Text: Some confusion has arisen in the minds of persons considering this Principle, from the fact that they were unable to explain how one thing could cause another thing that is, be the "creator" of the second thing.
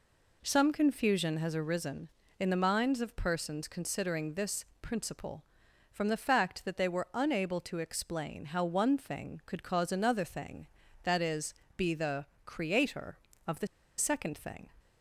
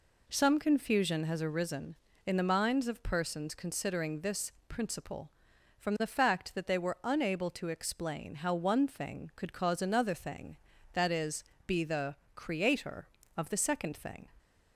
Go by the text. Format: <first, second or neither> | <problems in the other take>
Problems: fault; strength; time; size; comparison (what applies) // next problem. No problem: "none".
second | pauses between "this" and "Principle"; slight; at 4.6 s; 0.16 s long; slight in the second // pauses between "the" and "creator"; slight; at 12.2 s; 0.20 s long; slight in the second // pauses between "the" and "second"; slight; at 13.6 s; 0.30 s long